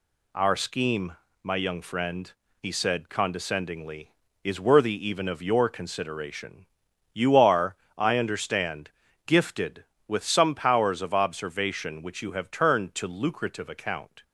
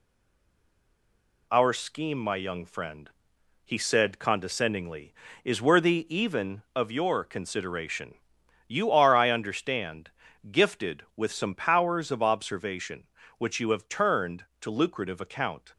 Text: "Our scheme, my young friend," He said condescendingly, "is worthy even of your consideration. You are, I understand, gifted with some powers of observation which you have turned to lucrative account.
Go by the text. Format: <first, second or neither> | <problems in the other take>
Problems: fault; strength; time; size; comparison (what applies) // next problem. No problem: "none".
first | stays silent before the first word; noticeable; until 1.4 s; 1.4 s long